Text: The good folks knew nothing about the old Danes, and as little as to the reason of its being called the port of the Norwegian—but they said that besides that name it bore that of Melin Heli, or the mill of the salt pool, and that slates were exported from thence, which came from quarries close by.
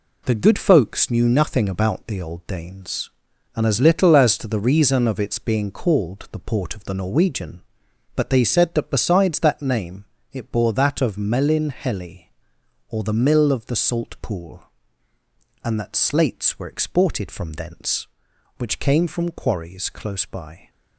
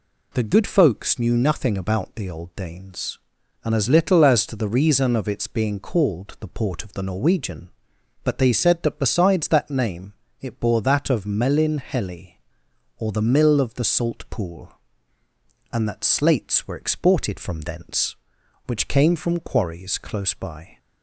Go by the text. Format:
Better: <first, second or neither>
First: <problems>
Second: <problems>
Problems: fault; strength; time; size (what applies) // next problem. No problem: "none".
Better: second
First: gets quieter; throughout; 6.5 dB // pauses between "name" and "it"; slight; at 10.0 s; 0.26 s long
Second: pauses between "name" and "it"; slight; at 10.1 s; 0.26 s long